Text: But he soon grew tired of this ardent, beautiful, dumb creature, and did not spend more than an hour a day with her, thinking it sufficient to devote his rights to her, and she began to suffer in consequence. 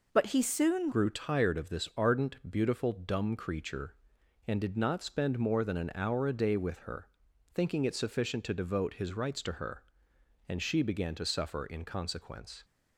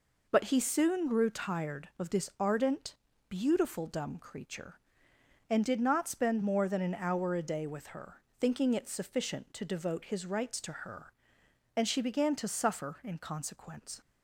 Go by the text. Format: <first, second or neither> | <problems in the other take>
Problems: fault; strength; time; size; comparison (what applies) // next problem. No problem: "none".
second | changes voice at "grew"; from 0.9 s on; 11.7 s long